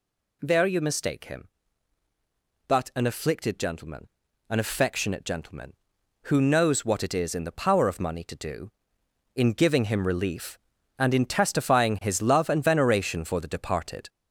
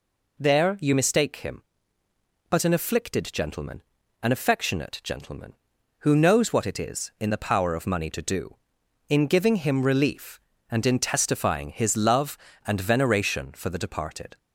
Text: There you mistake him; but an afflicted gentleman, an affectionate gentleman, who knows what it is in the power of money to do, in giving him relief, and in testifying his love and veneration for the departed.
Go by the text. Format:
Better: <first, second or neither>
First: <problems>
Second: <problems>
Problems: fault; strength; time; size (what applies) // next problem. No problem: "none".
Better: second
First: gets louder; noticeable; throughout; 5 dB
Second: none